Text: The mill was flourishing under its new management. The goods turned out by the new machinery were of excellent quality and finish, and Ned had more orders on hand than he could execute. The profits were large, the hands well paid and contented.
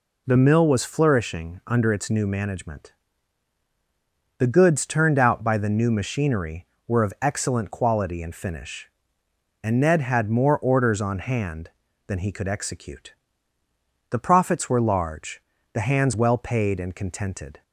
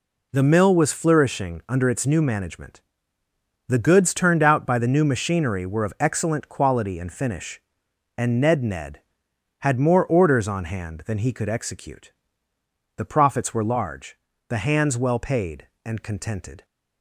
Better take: first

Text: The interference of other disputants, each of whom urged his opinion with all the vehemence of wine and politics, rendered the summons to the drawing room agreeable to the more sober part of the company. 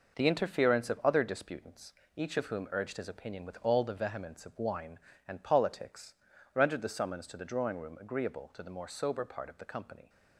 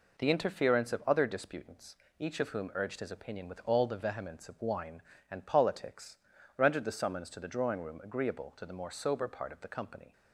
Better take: second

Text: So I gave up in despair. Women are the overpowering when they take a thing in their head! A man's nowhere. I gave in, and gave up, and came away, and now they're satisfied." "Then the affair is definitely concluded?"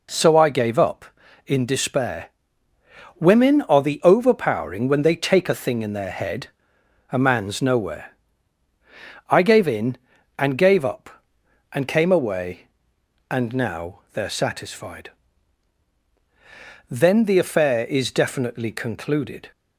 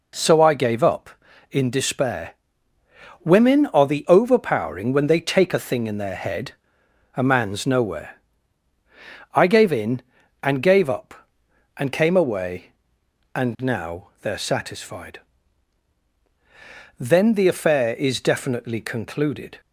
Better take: neither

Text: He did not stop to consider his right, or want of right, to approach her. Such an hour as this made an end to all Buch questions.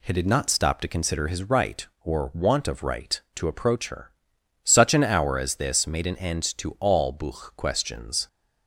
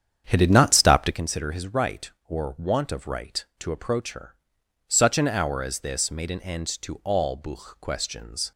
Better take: first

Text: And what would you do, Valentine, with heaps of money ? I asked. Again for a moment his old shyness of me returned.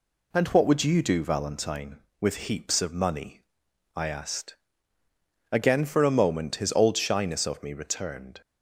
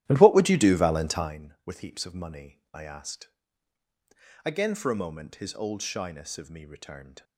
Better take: first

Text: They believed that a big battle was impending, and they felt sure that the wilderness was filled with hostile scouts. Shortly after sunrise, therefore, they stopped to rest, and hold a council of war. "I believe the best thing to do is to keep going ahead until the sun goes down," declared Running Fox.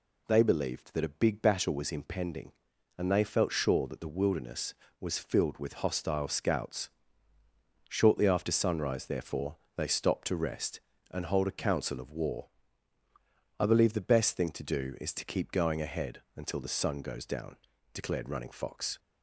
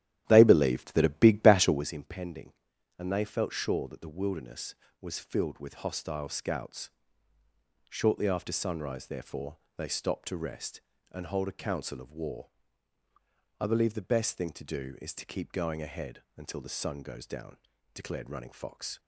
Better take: first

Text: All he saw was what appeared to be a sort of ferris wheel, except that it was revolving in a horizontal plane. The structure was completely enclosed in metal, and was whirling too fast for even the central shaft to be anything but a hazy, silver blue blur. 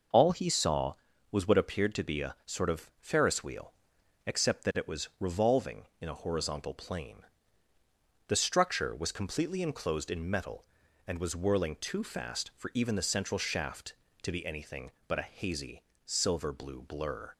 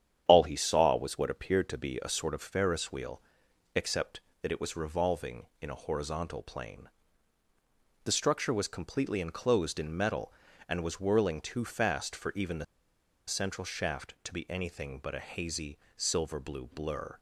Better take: first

